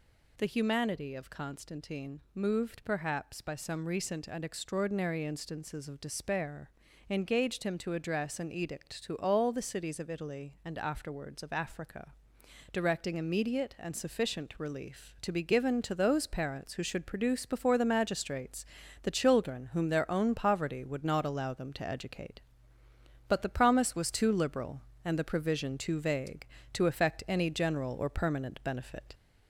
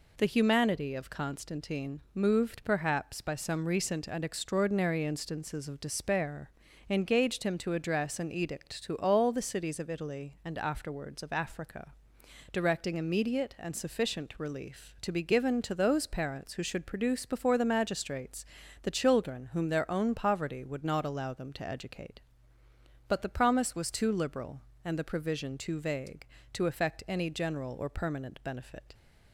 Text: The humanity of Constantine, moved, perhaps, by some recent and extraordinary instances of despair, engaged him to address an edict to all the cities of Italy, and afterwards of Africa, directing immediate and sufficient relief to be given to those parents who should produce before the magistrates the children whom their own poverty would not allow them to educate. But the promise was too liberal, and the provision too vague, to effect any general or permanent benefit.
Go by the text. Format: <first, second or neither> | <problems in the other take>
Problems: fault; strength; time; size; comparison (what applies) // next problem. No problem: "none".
second | gets louder; slight; throughout; 3 dB // pauses between "magistrates" and "the"; at 18.6 s; 0.38 s long; also in the second